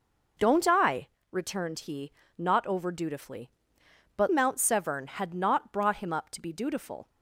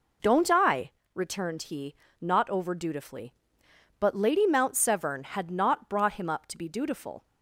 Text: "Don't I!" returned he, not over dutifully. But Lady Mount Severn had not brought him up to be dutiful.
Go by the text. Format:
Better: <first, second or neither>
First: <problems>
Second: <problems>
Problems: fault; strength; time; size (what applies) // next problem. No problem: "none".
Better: second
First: skips "Lady"; at 4.2 s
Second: none